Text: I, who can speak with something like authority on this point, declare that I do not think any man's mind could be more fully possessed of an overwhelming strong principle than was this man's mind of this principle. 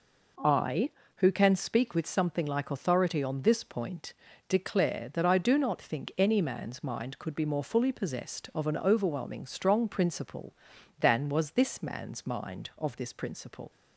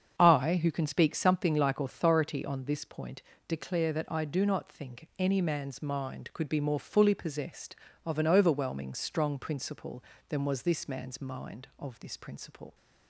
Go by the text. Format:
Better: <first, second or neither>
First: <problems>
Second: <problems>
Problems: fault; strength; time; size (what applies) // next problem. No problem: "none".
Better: first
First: none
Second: starts louder than the rest; strong; until 1.2 s; 7 dB // skips "with"; at 1.1 s